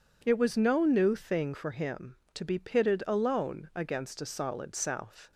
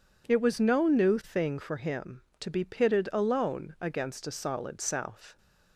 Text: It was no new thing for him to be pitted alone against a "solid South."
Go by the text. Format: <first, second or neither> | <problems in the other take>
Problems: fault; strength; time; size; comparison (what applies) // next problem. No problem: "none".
neither | none